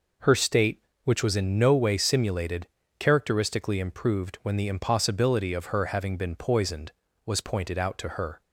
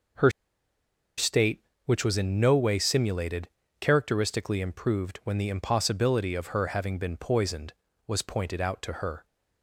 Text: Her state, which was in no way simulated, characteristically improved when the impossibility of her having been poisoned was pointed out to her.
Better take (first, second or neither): first